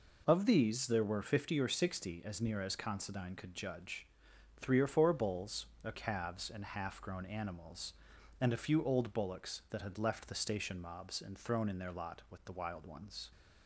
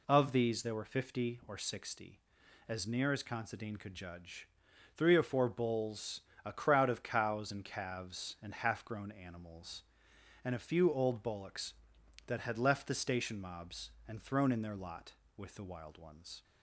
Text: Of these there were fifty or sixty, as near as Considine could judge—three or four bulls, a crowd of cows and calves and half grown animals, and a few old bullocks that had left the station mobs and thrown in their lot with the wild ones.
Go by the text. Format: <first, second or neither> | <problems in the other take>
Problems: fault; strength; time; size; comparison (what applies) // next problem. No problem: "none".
second | skips "crowd of cows and"; at 5.9 s